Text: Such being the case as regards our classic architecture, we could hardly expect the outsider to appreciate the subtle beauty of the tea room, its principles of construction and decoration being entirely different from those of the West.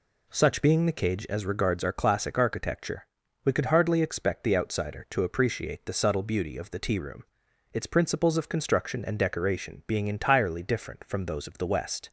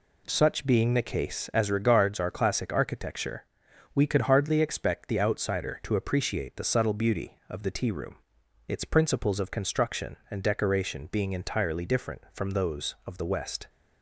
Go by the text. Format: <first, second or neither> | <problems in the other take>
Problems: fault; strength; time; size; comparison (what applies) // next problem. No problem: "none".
second | says "cage" for "case"; at 0.9 s